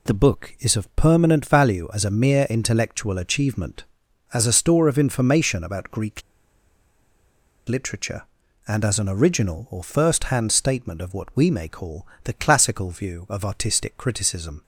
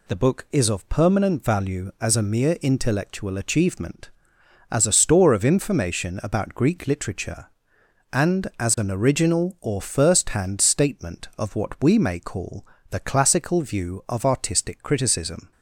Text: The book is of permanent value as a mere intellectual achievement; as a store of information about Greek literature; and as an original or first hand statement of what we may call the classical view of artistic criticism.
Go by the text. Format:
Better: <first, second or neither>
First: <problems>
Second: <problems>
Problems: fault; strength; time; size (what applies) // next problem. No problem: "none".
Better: second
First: pauses between "Greek" and "literature"; strong; at 6.2 s; 1.4 s long // pauses between "call" and "the"; slight; at 12.0 s; 0.18 s long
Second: pauses between "call" and "the"; slight; at 12.6 s; 0.24 s long